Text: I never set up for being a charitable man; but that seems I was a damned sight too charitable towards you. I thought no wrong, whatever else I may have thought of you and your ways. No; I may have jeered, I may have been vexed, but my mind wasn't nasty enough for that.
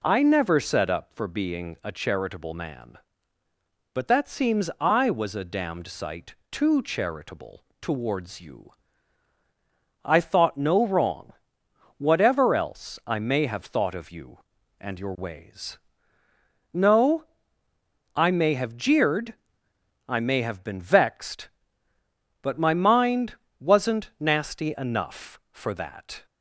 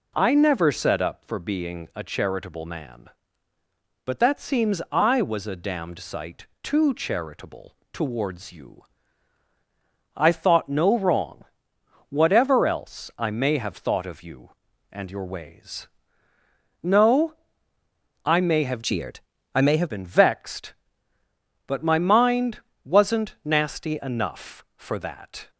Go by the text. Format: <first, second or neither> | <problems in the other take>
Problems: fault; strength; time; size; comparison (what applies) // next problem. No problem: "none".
first | pauses between "sight" and "too"; slight; at 6.4 s; 0.16 s long; slight in the first // pauses between "charitable" and "towards"; slight; at 7.7 s; 0.16 s long; slight in the first // changes voice from "jeered" to "have"; from 18.8 to 19.8 s; 1.0 s long // pauses between "mind" and "wasn't"; slight; at 22.6 s; 0.22 s long; slight in the first